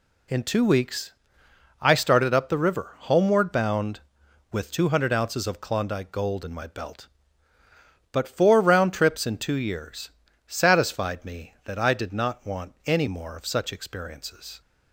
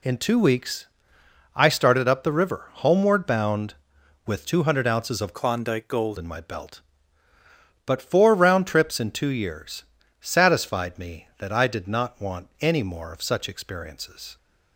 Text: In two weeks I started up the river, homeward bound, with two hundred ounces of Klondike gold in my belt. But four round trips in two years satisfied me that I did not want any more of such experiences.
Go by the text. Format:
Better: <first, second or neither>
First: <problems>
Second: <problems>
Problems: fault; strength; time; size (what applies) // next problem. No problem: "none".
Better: first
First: pauses between "weeks" and "I"; noticeable; at 1.1 s; 0.70 s long // pauses between "years" and "satisfied"; slight; at 10.1 s; 0.34 s long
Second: pauses between "weeks" and "I"; noticeable; at 0.8 s; 0.70 s long // changes voice from "Klondike" to "gold"; from 5.3 to 6.1 s; 0.8 s long // pauses between "years" and "satisfied"; slight; at 9.8 s; 0.34 s long